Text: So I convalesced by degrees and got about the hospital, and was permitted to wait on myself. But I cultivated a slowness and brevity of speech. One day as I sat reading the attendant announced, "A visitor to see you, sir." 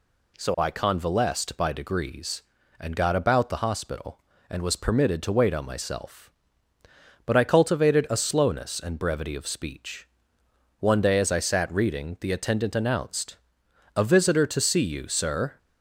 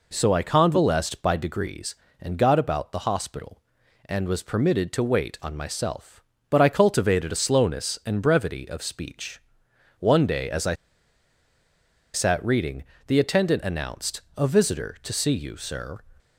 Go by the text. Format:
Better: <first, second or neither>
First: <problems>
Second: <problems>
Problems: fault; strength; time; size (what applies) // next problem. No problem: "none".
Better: first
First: none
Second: pauses between "I" and "sat"; strong; at 10.7 s; 1.3 s long // pauses between "reading" and "the"; slight; at 12.8 s; 0.24 s long